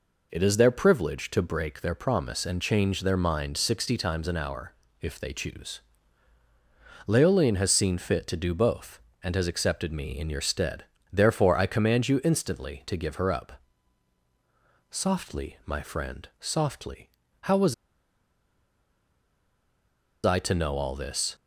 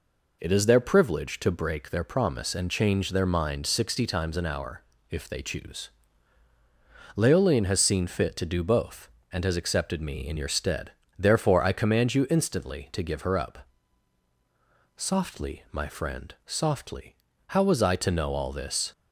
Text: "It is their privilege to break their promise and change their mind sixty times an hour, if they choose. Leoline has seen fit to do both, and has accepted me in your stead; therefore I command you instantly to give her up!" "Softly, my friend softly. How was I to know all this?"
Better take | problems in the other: second | pauses between "was" and "I"; strong; at 17.7 s; 2.5 s long

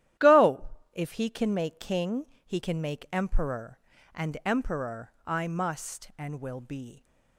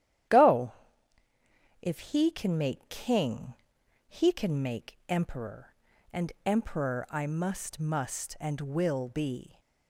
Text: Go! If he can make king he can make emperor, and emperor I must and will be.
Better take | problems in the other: first | starts louder than the rest; strong; until 2.4 s; 11.5 dB; strong in the first // pauses between "king" and "he"; noticeable; at 3.5 s; 0.56 s long; slight in the first // says "must" twice; at 7.7 s

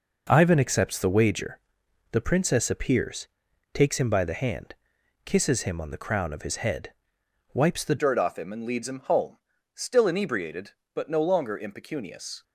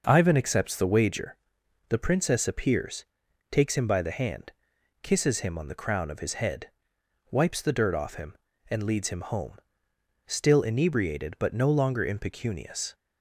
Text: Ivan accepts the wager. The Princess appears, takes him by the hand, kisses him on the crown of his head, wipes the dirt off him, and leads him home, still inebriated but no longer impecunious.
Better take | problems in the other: second | changes voice at "dirt"; from 7.9 s on; 4.5 s long

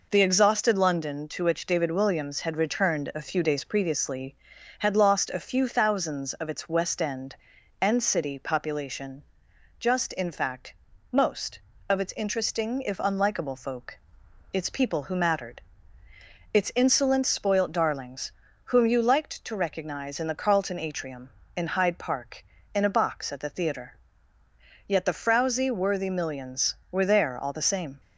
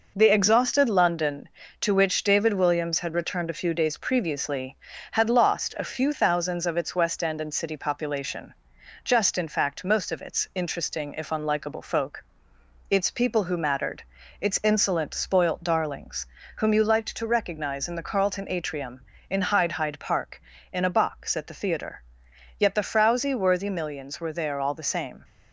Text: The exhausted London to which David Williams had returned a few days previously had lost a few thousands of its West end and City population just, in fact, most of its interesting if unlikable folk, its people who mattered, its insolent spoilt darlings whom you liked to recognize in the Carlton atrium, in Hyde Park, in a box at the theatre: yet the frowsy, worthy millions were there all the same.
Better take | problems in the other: first | pauses between "population" and "just"; noticeable; at 8.5 s; 0.52 s long; noticeable in the first // pauses between "darlings" and "whom"; slight; at 16.2 s; 0.30 s long; slight in the first // says "Hyde" twice; at 19.7 s

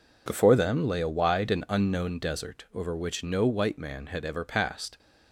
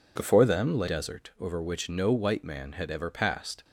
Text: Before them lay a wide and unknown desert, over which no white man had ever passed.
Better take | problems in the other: first | skips "a wide and unknown"; at 0.8 s

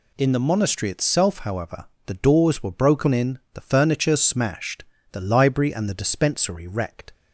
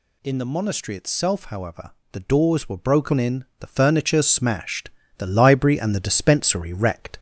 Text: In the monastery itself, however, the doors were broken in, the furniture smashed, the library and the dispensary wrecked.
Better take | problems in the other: first | gets louder; slight; throughout; 2.5 dB

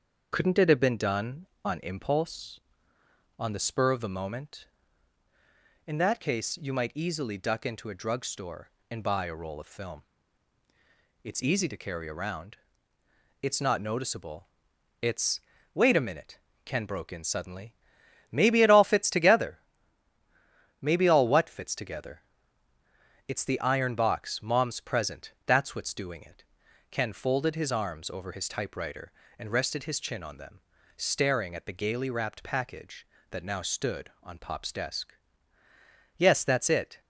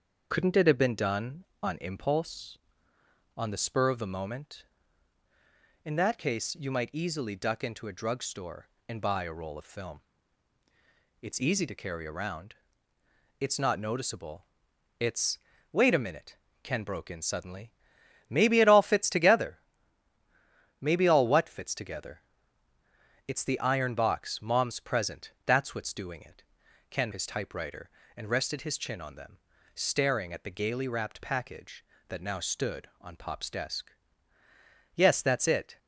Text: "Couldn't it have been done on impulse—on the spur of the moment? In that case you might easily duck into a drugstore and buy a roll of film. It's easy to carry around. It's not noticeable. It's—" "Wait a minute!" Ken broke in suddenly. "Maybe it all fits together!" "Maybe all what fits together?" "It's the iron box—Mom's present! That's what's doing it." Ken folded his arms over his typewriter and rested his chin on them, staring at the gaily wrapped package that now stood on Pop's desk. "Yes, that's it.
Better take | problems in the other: first | starts louder than the rest; until 1.3 s; 6.5 dB; also in the first // skips "folded his arms over"; at 27.1 s

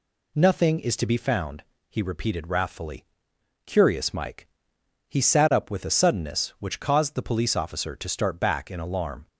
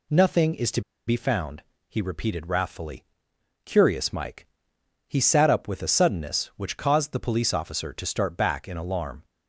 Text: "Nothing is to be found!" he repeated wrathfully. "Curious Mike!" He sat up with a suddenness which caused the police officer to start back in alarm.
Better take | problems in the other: first | pauses between "to" and "be"; slight; at 0.8 s; 0.27 s long

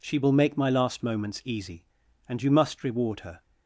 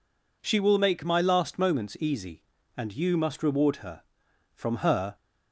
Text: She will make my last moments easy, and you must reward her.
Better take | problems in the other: first | goes on to say "From her"; noticeable; from 4.5 s on; 0.62 s long

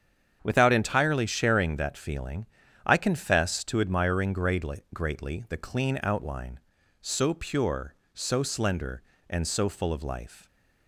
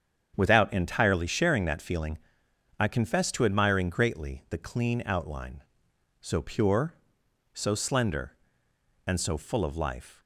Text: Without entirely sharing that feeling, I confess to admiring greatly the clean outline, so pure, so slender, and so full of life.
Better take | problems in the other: second | starts louder than the rest; strong; until 1.4 s; 8 dB; strong in the second // says "greatly" twice; at 4.9 s

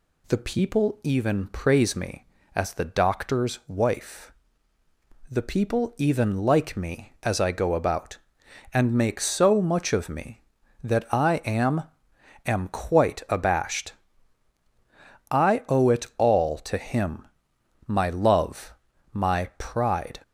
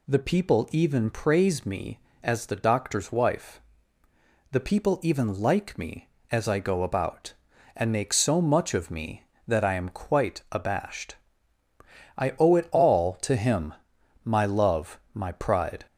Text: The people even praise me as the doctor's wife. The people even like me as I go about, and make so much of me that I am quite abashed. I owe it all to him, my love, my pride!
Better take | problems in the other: second | says "am" twice; at 12.4 s

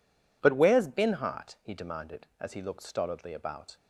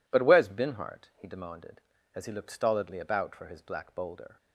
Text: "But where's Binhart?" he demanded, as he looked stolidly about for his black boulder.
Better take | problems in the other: second | stops before "for his black boulder"; at 3.7 s

